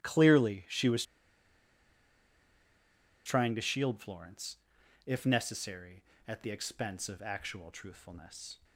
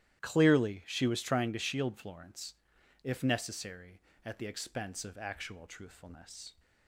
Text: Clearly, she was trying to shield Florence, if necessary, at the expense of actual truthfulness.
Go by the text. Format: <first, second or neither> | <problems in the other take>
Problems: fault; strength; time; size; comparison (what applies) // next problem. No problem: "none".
second | starts louder than the rest; strong; until 1.0 s; 12.5 dB; strong in the second // pauses between "was" and "trying"; strong; at 1.0 s; 2.2 s long